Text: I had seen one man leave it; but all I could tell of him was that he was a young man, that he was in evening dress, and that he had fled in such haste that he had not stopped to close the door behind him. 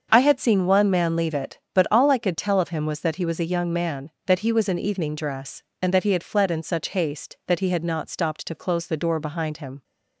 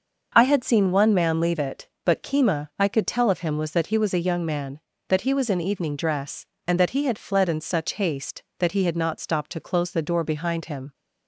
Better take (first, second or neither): first